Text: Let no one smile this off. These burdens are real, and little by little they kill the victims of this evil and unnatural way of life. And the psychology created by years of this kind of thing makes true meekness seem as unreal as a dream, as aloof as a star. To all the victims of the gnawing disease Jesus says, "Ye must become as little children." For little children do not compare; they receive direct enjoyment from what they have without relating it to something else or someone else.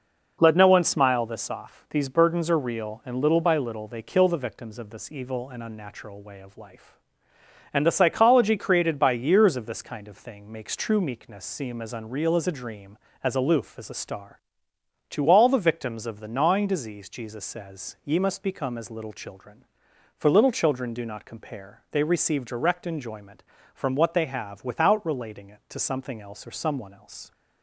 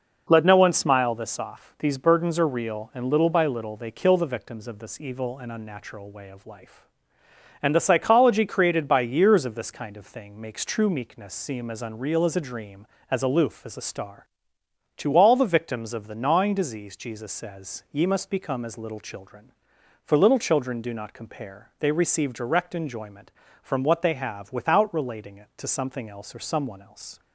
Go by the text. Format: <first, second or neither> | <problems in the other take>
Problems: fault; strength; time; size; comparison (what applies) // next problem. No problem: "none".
neither | none